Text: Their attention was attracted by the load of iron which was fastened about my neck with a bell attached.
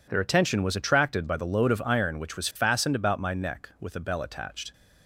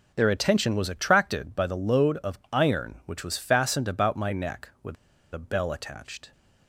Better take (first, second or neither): first